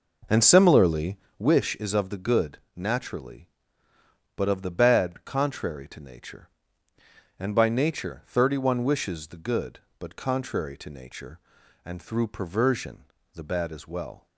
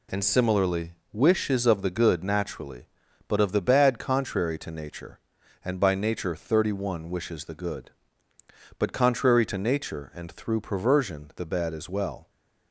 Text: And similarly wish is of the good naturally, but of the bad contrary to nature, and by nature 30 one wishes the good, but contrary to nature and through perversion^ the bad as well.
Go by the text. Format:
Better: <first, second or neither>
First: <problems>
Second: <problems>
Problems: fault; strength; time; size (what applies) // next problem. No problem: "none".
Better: second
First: starts louder than the rest; noticeable; until 1.5 s; 5.5 dB // pauses between "similarly" and "wish"; slight; at 1.1 s; 0.20 s long // pauses between "good" and "naturally"; slight; at 2.5 s; 0.16 s long // pauses between "perversion" and "the"; slight; at 13.0 s; 0.30 s long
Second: pauses between "similarly" and "wish"; slight; at 0.9 s; 0.18 s long